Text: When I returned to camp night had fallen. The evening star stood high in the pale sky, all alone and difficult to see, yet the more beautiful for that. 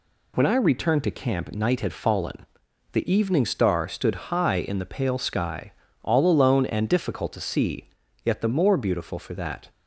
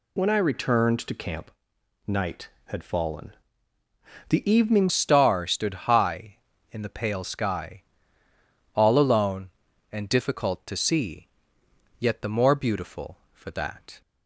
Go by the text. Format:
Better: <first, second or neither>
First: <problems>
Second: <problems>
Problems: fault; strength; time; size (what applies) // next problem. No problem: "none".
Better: first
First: none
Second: pauses between "camp" and "night"; noticeable; at 1.5 s; 0.56 s long // changes voice at "star"; from 4.8 s on; 9.2 s long